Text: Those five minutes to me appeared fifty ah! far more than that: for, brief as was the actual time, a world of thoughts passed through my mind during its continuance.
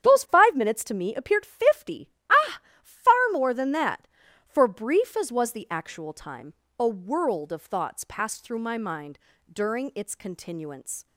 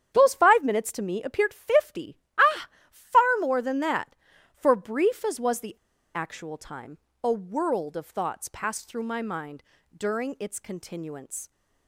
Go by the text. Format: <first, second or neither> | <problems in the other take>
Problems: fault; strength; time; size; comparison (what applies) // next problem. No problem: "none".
first | starts louder than the rest; strong; until 1.1 s; 9 dB; strong in the first // pauses between "fifty" and "ah"; slight; at 2.1 s; 0.22 s long; slight in the first // pauses between "the" and "actual"; at 5.7 s; 0.40 s long // pauses between "mind" and "during"; slight; at 9.6 s; 0.32 s long; slight in the first